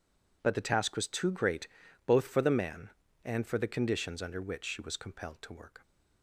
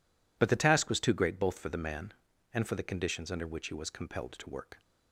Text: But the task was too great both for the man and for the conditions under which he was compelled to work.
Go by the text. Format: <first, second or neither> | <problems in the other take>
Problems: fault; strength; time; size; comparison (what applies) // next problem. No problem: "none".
second | pauses between "great" and "both"; at 1.6 s; 0.38 s long // says "she" for "he"; at 4.6 s